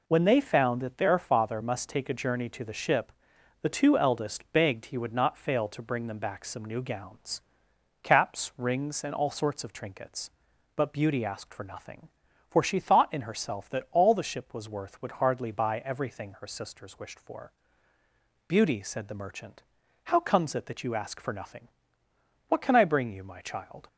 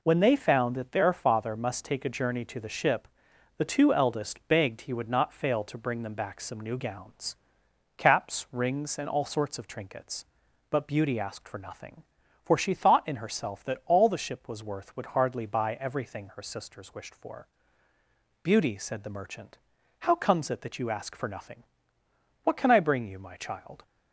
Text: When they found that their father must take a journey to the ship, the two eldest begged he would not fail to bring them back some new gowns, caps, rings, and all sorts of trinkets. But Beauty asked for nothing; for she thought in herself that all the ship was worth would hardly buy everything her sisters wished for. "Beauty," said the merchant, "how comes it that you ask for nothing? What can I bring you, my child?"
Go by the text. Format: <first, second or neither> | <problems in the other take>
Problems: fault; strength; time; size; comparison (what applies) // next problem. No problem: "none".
neither | none